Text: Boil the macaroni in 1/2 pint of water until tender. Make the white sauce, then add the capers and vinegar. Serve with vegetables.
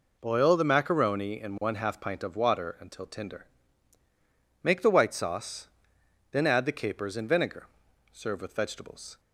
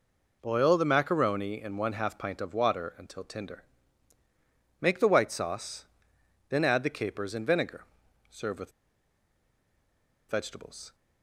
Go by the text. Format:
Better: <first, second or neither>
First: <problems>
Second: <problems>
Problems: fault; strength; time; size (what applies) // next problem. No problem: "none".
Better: first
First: none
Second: pauses between "with" and "vegetables"; strong; at 8.7 s; 1.5 s long